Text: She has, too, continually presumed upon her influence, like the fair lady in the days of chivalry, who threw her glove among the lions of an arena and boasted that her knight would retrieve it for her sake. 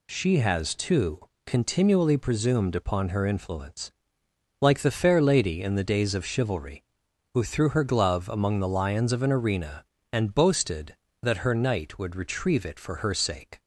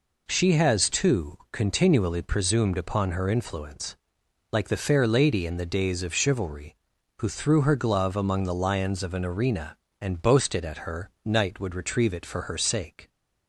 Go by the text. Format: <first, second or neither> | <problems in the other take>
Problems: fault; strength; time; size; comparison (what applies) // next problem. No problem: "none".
first | says "at" for "that"; at 10.6 s